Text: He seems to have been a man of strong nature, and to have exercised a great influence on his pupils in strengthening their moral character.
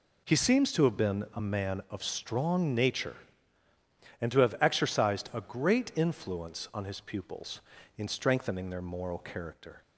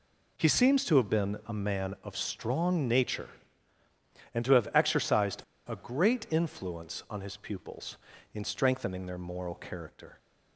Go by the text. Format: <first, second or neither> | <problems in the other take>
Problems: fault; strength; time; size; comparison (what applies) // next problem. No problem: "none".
first | pauses between "exercised" and "a"; slight; at 5.4 s; 0.25 s long